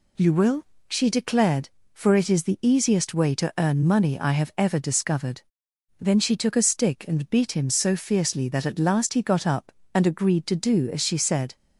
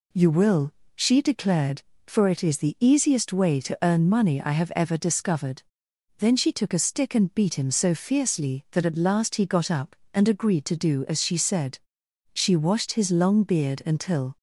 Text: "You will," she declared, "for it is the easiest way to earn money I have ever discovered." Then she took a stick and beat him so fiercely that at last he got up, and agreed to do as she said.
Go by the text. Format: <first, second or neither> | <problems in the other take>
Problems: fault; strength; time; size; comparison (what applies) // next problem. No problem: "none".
first | goes on to say "She washed his long beard until"; strong; from 12.3 s on; 2.0 s long